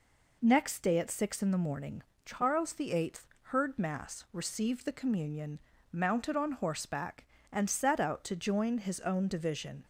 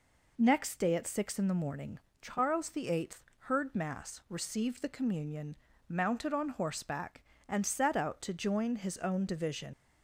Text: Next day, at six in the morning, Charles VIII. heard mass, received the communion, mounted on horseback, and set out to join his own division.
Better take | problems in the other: first | leaves "division" unfinished; at 9.7 s; 90 ms

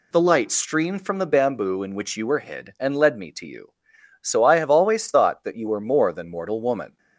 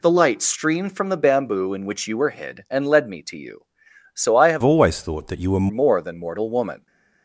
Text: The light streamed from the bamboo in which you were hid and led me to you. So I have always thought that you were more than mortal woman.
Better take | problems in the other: first | changes voice from "always" to "were"; from 4.6 to 5.6 s; 1.0 s long

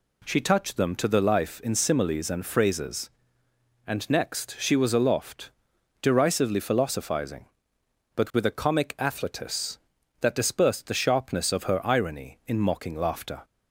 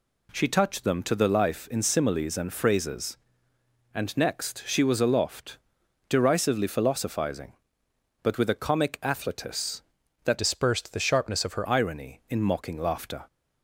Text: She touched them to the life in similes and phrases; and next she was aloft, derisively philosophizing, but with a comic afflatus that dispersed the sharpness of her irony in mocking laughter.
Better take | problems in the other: first | changes voice from "dispersed" to "her"; from 10.3 to 11.6 s; 1.3 s long

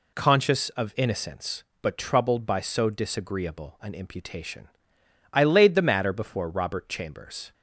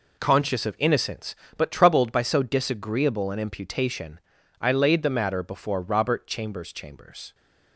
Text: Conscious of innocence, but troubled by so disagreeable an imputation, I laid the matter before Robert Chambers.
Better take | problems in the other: first | says "Chambers" twice; at 6.7 s

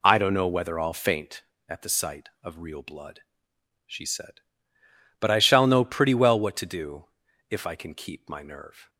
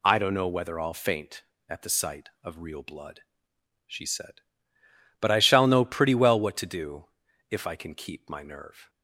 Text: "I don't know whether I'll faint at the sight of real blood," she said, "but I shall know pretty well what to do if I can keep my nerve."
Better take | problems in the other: second | starts louder than the rest; slight; until 1.6 s; 2 dB // pauses between "do" and "if"; noticeable; at 7.0 s; 0.46 s long; noticeable in the second

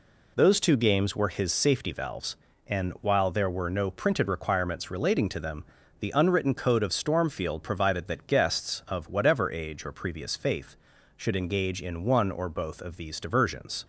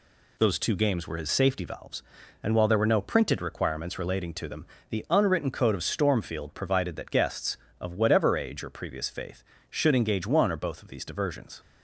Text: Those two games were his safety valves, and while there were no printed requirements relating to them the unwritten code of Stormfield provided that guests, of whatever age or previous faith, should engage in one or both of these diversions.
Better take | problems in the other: first | pauses between "them" and "the"; slight; at 4.6 s; 0.24 s long; slight in the first // skips "in"; at 10.2 s

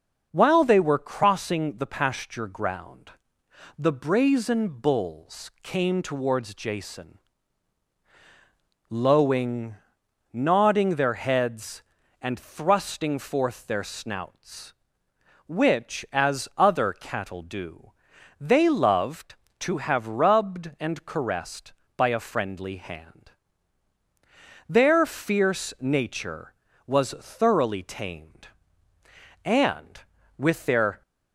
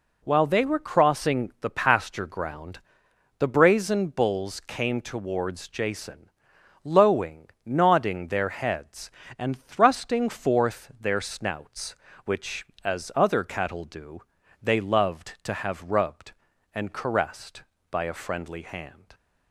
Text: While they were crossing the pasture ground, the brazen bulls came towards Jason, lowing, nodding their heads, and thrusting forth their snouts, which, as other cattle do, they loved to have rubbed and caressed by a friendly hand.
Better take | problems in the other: second | starts louder than the rest; noticeable; until 1.3 s; 6 dB // goes on to say "Their fierce nature was thoroughly tamed and with their"; strong; from 24.6 s on; 6.3 s long

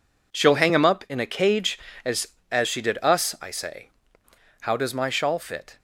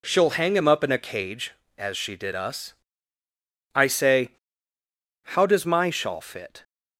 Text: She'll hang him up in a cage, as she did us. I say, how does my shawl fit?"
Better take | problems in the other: second | says "as" twice; at 2.5 s

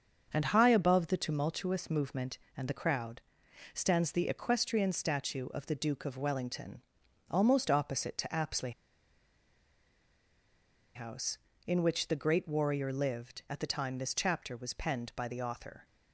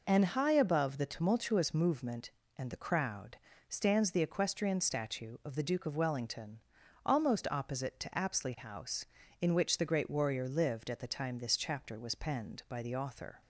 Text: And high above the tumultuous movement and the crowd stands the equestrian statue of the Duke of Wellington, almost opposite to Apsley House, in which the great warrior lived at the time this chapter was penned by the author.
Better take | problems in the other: second | starts louder than the rest; until 1.3 s; 6.5 dB // pauses between "crowd" and "stands"; noticeable; at 3.2 s; 0.52 s long; slight in the second // pauses between "Apsley" and "House"; strong; at 8.7 s; 2.2 s long

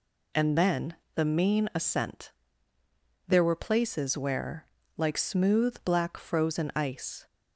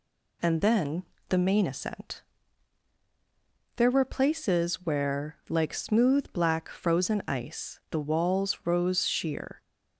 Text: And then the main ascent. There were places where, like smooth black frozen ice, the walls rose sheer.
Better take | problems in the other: second | pauses between "then" and "the"; slight; at 0.9 s; 0.20 s long; slight in the second // stops before "the walls rose sheer"; at 7.2 s

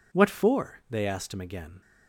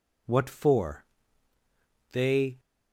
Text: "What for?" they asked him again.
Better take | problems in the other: first | stops before "asked him again"; at 2.5 s

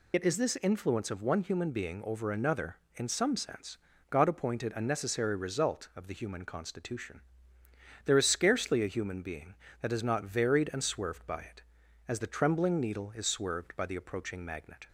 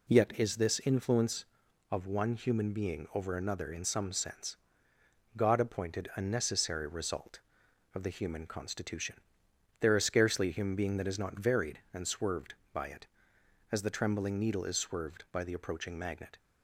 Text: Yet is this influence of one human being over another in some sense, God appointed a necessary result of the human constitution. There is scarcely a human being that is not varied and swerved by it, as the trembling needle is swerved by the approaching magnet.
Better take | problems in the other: second | loses the start of "Yet"; at 0.1 s; 50 ms

